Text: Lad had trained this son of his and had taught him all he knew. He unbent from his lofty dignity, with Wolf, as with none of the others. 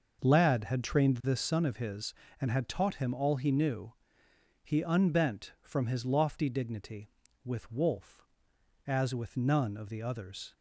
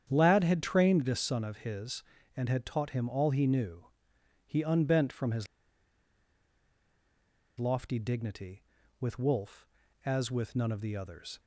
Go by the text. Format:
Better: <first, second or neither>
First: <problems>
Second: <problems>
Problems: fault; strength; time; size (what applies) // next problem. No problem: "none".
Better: first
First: none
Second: starts louder than the rest; strong; until 1.1 s; 8.5 dB // pauses between "his" and "lofty"; strong; at 5.4 s; 2.1 s long